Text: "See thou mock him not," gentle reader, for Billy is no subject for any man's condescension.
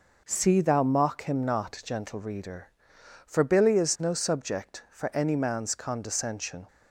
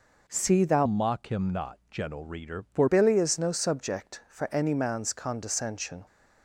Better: first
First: none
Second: changes voice from "mock" to "for"; from 0.8 to 2.8 s; 2.0 s long

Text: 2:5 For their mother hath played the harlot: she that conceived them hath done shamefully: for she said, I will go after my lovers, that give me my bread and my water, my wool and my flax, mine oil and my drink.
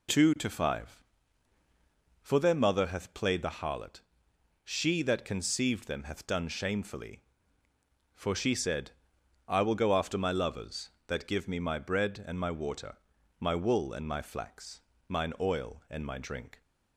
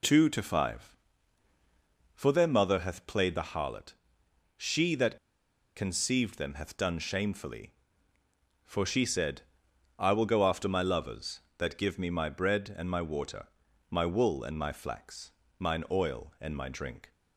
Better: first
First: none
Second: pauses between "that" and "conceived"; noticeable; at 5.1 s; 0.60 s long

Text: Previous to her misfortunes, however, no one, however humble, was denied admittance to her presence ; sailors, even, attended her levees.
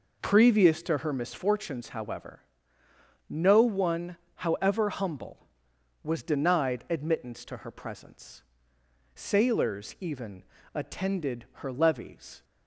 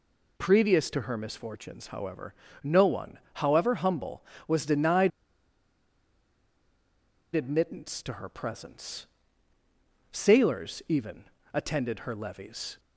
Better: first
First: none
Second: pauses between "denied" and "admittance"; strong; at 5.1 s; 2.2 s long

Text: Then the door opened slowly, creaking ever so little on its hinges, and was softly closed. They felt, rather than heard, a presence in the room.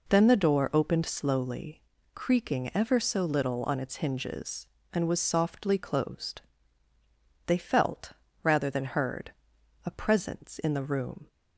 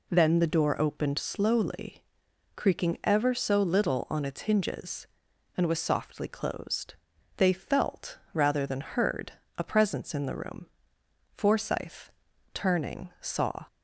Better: first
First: none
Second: goes on to say "Forsyth turning saw"; strong; from 11.3 s on; 2.3 s long

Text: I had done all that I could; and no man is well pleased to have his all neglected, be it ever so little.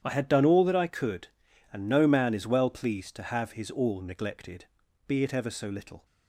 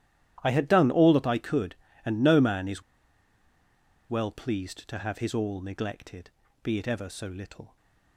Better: first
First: starts louder than the rest; strong; until 1.0 s; 10 dB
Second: starts louder than the rest; strong; until 1.4 s; 12.5 dB // pauses between "is" and "well"; strong; at 2.8 s; 1.2 s long

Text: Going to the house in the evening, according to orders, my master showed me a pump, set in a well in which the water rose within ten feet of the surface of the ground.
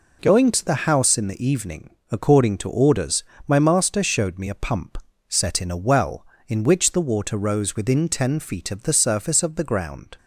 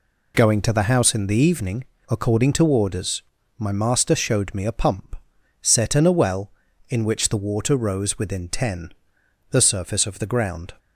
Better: first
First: none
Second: skips "feet of"; at 9.2 s

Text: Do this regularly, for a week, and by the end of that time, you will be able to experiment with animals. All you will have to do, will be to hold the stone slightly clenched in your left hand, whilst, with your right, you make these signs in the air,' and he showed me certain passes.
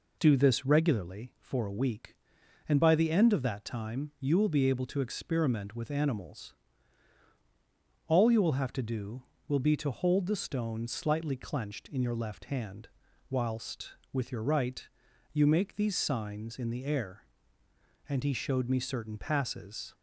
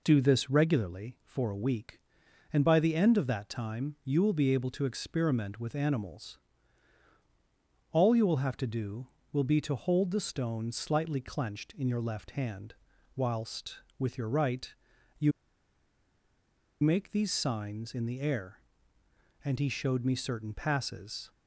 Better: first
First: none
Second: pauses between "you" and "make"; strong; at 15.3 s; 1.5 s long

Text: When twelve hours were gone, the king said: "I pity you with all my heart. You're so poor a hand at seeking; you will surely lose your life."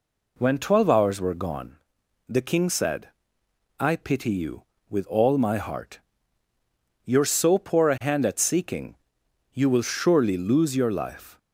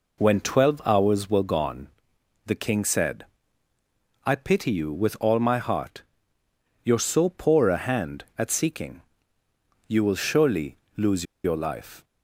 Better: first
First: none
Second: pauses between "surely" and "lose"; slight; at 10.7 s; 0.22 s long // pauses between "lose" and "your"; slight; at 11.2 s; 0.21 s long

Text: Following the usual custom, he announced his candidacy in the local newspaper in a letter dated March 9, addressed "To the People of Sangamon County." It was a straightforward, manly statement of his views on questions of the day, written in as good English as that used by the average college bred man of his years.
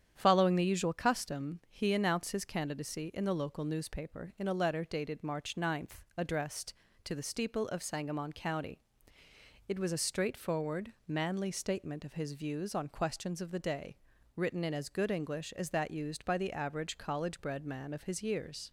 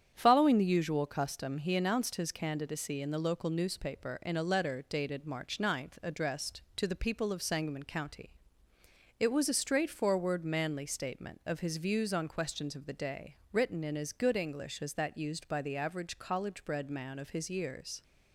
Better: second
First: starts louder than the rest; strong; until 1.1 s; 9 dB // says "Steeple" for "People"; at 7.2 s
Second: starts louder than the rest; strong; until 1.1 s; 8.5 dB

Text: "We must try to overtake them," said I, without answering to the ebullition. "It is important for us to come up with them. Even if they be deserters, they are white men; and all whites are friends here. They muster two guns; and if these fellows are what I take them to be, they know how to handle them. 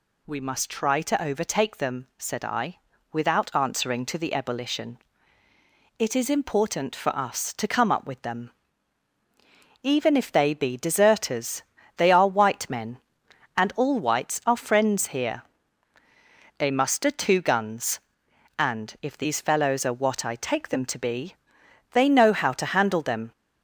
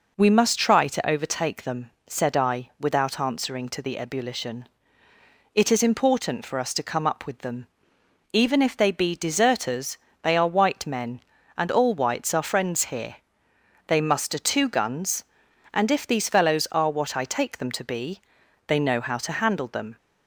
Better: neither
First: none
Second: none

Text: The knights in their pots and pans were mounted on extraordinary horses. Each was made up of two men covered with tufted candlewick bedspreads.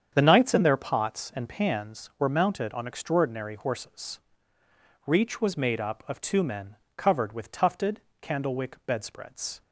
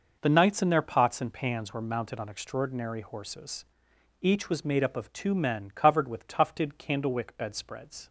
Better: second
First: starts louder than the rest; strong; until 1.1 s; 8 dB // says "Reach" for "Each"; at 5.0 s // pauses between "men" and "covered"; slight; at 6.7 s; 0.20 s long // pauses between "tufted" and "candlewick"; slight; at 7.9 s; 0.22 s long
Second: none

